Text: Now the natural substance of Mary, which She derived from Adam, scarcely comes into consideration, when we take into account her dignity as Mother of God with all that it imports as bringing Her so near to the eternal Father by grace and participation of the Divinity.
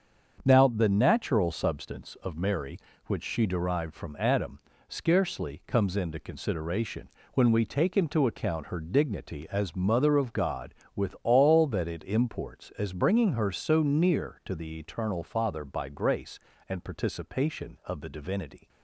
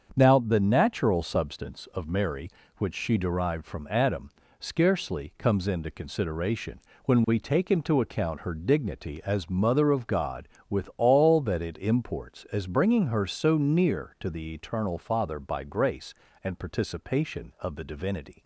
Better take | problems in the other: neither | starts louder than the rest; the same in both

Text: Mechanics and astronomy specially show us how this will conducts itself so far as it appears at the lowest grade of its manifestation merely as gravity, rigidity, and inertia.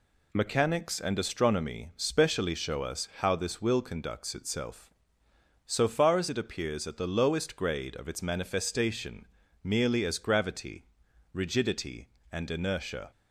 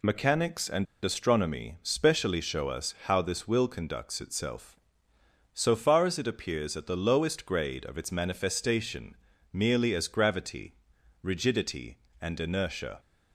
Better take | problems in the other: first | pauses between "and" and "astronomy"; slight; at 0.8 s; 0.18 s long // pauses between "manifestation" and "merely"; slight; at 9.1 s; 0.36 s long; slight in the first

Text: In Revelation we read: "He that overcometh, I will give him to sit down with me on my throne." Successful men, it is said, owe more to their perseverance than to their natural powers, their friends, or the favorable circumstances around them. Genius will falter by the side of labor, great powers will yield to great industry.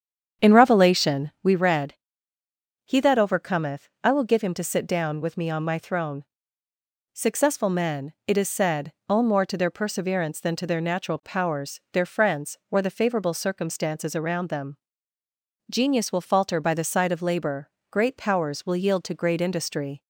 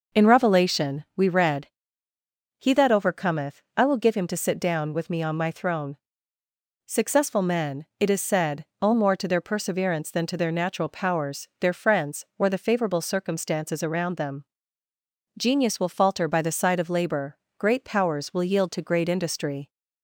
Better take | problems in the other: second | starts louder than the rest; strong; until 1.6 s; 8 dB

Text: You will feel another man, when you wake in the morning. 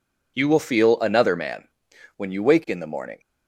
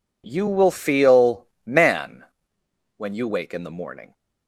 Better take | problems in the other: first | skips "another"; at 1.5 s

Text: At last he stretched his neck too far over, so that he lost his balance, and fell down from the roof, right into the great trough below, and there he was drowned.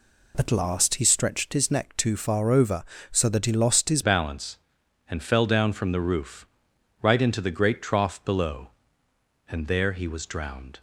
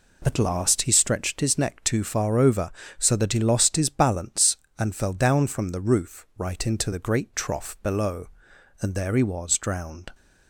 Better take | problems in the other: second | changes voice at "balance"; from 4.0 s on; 6.8 s long

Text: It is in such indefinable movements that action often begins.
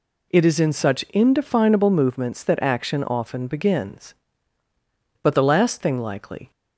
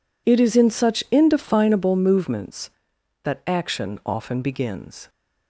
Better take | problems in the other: second | goes on to say "But the last thing likely"; noticeable; from 5.2 s on; 1.2 s long

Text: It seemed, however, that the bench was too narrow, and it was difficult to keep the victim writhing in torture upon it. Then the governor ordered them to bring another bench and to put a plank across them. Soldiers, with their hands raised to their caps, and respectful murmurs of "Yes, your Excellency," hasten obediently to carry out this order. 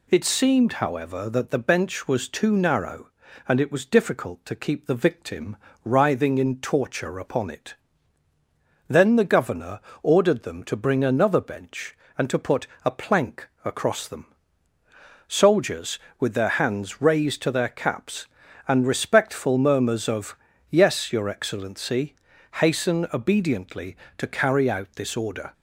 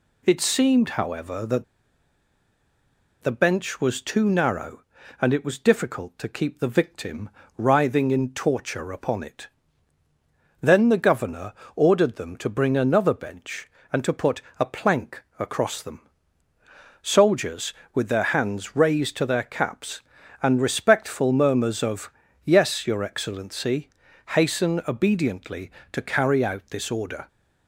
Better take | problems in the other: first | pauses between "that" and "the"; strong; at 1.6 s; 1.5 s long // pauses between "victim" and "writhing"; slight; at 7.2 s; 0.28 s long; slight in the first // pauses between "governor" and "ordered"; slight; at 11.5 s; 0.22 s long; slight in the first // pauses between "put" and "a"; slight; at 14.4 s; 0.18 s long; slight in the first // pauses between "plank" and "across"; slight; at 15.2 s; 0.16 s long; slight in the first // pauses between "of" and "Yes"; slight; at 22.1 s; 0.32 s long; slight in the first

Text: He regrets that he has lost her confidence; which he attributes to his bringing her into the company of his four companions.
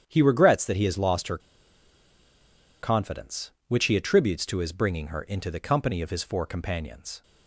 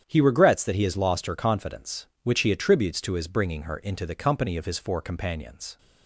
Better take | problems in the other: second | starts louder than the rest; strong; until 1.0 s; 9 dB; strong in the second // pauses between "her" and "confidence"; strong; at 1.3 s; 1.4 s long

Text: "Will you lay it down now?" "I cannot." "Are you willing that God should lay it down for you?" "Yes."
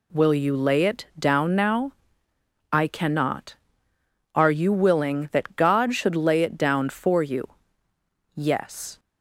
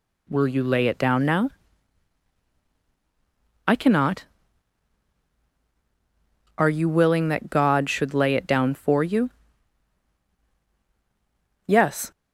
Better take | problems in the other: neither | none

